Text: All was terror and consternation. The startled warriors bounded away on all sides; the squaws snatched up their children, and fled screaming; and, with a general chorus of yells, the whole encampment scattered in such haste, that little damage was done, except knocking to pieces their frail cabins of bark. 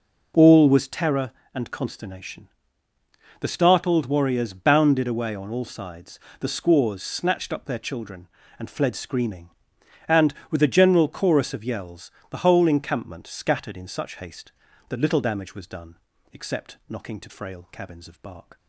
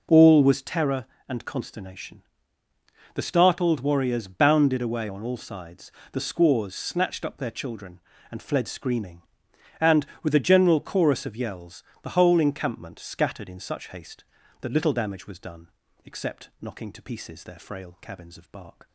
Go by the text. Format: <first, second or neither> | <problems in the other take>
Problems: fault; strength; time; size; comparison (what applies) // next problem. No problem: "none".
second | skips "pieces their"; at 17.2 s